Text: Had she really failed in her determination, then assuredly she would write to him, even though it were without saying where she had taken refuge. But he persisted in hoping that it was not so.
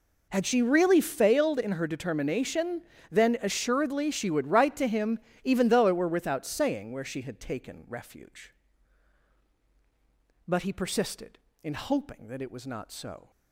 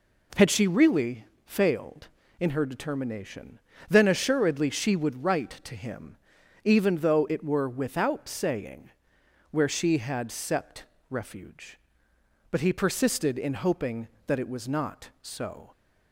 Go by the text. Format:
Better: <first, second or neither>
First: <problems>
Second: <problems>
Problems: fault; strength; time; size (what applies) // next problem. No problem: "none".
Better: first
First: none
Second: pauses between "really" and "failed"; slight; at 1.2 s; 0.20 s long // pauses between "saying" and "where"; noticeable; at 8.8 s; 0.62 s long // says "sept" for "taken"; at 10.2 s